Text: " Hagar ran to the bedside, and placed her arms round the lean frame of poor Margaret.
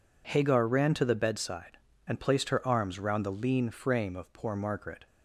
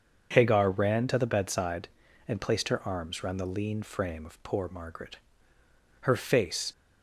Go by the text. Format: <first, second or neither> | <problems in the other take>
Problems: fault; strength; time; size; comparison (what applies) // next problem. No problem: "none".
first | starts louder than the rest; until 1.3 s; 6.5 dB // goes on to say "Her face"; noticeable; from 6.0 s on; 0.68 s long